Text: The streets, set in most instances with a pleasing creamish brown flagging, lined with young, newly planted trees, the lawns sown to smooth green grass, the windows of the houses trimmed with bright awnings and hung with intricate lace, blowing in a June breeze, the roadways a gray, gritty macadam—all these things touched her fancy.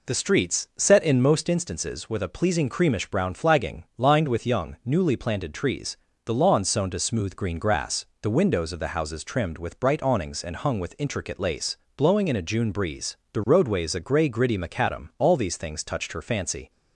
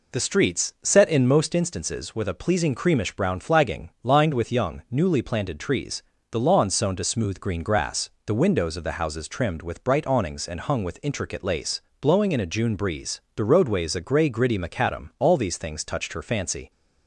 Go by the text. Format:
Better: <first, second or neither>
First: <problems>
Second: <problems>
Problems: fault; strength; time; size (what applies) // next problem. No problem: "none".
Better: neither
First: none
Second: none